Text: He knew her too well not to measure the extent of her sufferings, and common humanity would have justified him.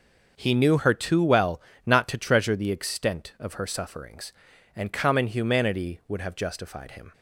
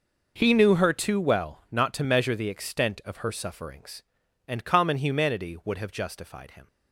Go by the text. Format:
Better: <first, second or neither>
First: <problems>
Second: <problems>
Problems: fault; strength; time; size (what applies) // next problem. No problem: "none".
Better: second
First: starts louder than the rest; noticeable; until 1.3 s; 6 dB // pauses between "well" and "not"; slight; at 1.6 s; 0.26 s long // says "treasure" for "measure"; at 2.1 s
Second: none